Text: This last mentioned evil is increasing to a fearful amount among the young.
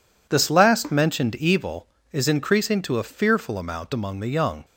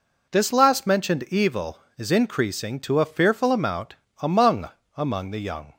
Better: first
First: none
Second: pauses between "amount" and "among"; slight; at 3.9 s; 0.24 s long // says "among" twice; at 4.9 s

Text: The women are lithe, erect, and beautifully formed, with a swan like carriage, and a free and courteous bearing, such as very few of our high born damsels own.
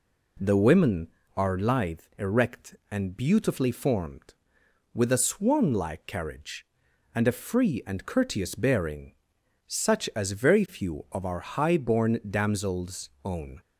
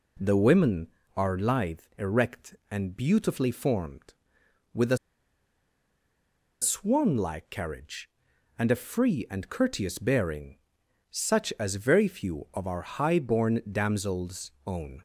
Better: first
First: none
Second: pauses between "a" and "swan"; strong; at 4.9 s; 1.6 s long

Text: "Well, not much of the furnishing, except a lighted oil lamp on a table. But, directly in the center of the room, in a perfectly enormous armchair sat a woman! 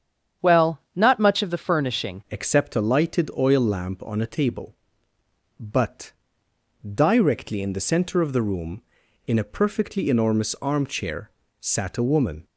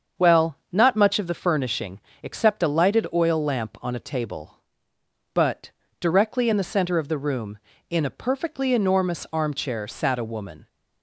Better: second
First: starts louder than the rest; strong; until 1.5 s; 8.5 dB // changes voice at "except"; from 2.3 s on; 10.1 s long // pauses between "armchair" and "sat"; slight; at 11.3 s; 0.28 s long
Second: starts louder than the rest; until 1.3 s; 7 dB

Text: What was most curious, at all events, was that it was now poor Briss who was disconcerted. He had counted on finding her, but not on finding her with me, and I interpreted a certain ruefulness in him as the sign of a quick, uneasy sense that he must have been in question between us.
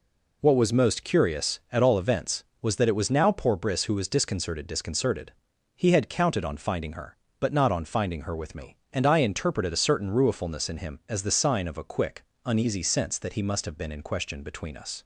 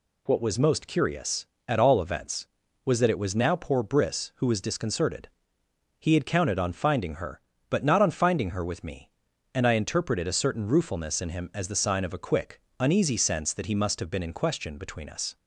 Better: second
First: says "disconcerted" twice; at 4.6 s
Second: none

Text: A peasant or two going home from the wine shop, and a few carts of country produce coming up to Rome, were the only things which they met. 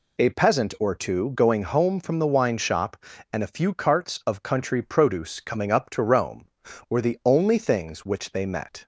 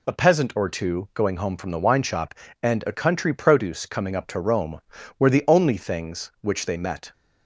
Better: first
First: none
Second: skips "few carts of"; at 2.9 s

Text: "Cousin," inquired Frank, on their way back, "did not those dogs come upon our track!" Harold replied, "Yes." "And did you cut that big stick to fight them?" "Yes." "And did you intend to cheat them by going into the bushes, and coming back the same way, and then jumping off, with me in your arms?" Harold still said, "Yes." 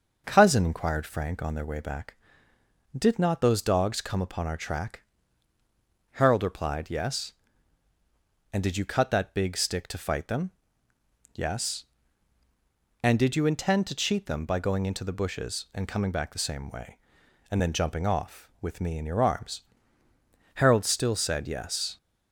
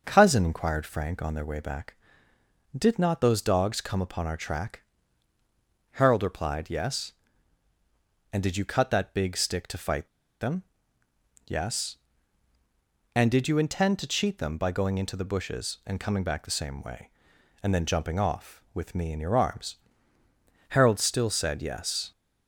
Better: first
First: starts louder than the rest; until 1.2 s; 6 dB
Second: starts louder than the rest; noticeable; until 1.0 s; 6 dB // pauses between "fight" and "them"; slight; at 10.0 s; 0.33 s long

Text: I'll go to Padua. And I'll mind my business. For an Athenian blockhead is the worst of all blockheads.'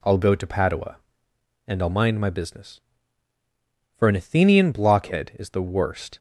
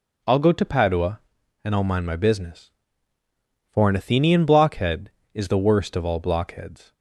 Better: second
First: stops before "of all blockheads"; at 6.1 s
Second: none

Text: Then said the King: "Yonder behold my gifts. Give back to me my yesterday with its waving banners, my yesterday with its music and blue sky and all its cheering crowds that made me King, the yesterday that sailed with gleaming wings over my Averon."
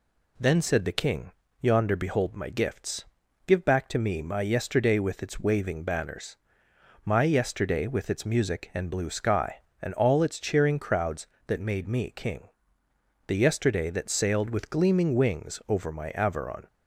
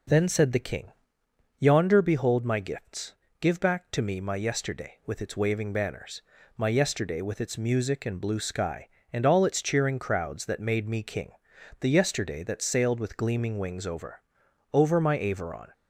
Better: first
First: none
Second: says "over" twice; at 14.7 s

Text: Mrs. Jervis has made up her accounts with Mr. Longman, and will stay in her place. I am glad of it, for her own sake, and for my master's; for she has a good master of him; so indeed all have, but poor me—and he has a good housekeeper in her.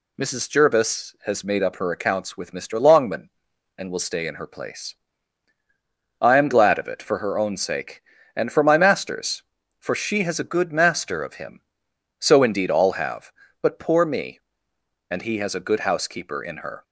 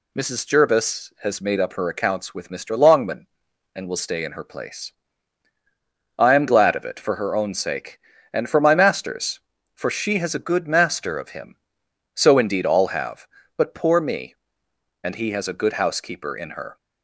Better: neither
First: none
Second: none

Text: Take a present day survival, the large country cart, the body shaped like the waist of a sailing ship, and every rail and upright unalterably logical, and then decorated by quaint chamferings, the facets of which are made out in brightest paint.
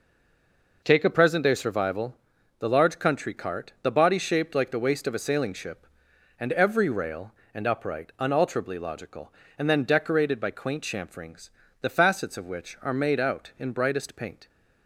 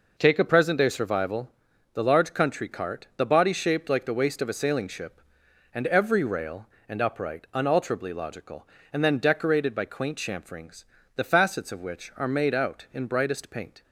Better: second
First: stays silent before the first word; slight; until 0.8 s; 0.8 s long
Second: none

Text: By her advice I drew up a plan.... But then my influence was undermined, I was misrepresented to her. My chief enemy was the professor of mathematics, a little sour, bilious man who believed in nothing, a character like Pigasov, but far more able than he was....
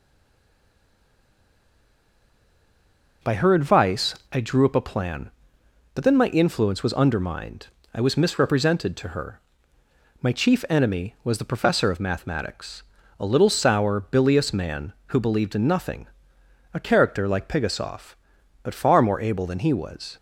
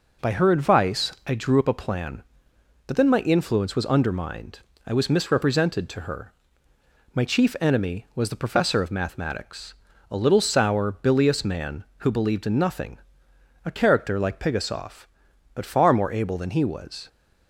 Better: second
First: stays silent before the first word; strong; until 3.2 s; 3.2 s long // pauses between "advice" and "I"; slight; at 4.1 s; 0.17 s long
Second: none

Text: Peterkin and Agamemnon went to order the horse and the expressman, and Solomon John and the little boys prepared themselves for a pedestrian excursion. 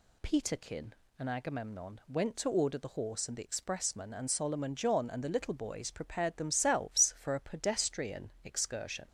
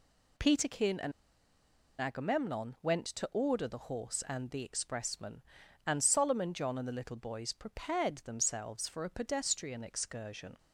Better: first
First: none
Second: pauses between "and" and "Agamemnon"; noticeable; at 1.1 s; 0.89 s long

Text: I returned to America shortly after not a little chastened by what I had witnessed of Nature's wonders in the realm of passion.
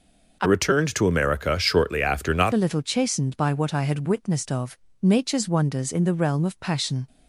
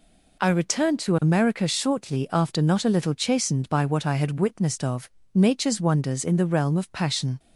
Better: second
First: changes voice from "returned" to "not"; from 0.4 to 2.5 s; 2.1 s long // pauses between "of" and "Nature's"; slight; at 4.7 s; 0.24 s long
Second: pauses between "of" and "Nature's"; slight; at 5.0 s; 0.24 s long

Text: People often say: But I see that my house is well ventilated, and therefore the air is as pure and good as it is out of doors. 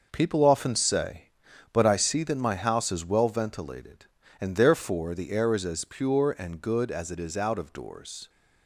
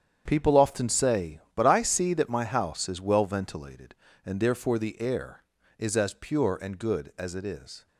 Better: first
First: none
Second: starts louder than the rest; strong; until 1.2 s; 8.5 dB // stops before "out of doors"; at 7.8 s

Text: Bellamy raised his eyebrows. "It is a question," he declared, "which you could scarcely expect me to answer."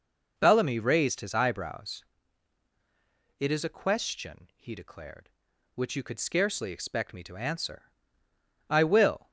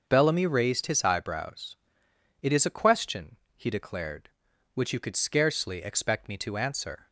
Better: second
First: goes on to say "I will"; noticeable; from 8.6 s on; 0.62 s long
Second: none

